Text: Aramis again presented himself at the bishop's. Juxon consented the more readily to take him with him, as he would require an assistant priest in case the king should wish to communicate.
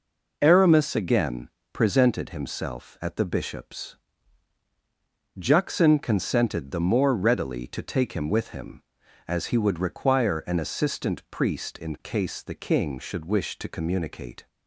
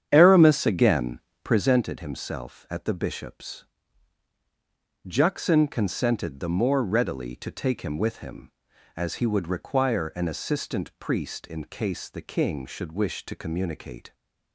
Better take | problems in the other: first | starts louder than the rest; strong; until 1.7 s; 9 dB // pauses between "again" and "presented"; slight; at 1.1 s; 0.24 s long; slight in the first

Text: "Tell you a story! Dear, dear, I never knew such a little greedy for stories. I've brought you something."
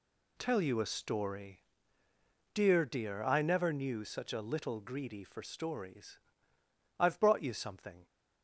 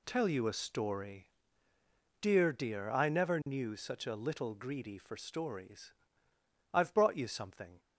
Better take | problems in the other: neither | none

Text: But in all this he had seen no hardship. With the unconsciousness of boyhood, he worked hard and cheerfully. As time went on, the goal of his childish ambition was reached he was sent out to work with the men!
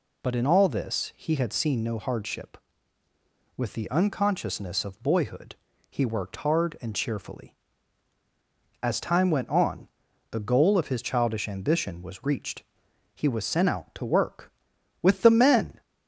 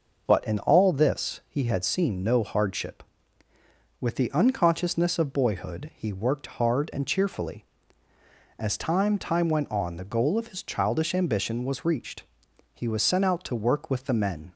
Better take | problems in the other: first | says "time" twice; at 9.1 s // pauses between "reached" and "he"; noticeable; at 12.2 s; 0.52 s long; noticeable in the first

